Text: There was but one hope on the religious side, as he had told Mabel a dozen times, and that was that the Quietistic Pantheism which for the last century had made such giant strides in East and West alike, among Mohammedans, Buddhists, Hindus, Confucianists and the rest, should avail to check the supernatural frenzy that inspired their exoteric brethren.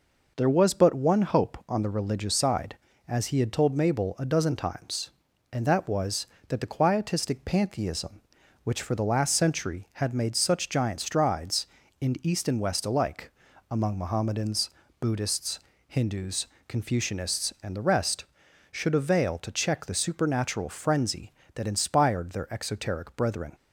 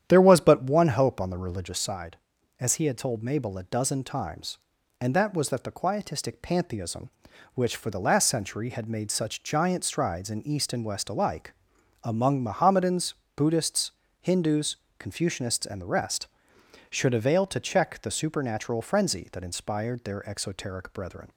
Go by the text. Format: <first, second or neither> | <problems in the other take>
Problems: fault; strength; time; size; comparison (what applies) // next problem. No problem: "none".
first | starts louder than the rest; strong; until 1.8 s; 9.5 dB